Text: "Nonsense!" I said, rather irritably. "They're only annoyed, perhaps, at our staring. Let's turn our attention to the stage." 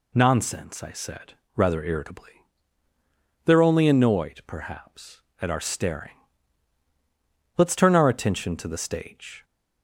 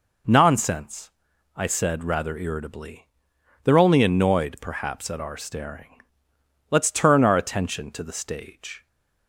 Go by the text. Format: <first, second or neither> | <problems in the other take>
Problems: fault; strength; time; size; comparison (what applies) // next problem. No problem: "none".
neither | none